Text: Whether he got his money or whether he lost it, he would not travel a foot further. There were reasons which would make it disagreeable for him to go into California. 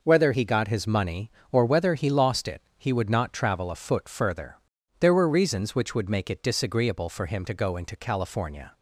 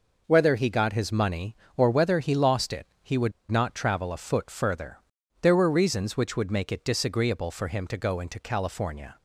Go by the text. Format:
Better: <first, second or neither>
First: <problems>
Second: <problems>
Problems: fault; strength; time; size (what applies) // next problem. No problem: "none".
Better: first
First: none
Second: pauses between "would" and "not"; slight; at 3.3 s; 0.18 s long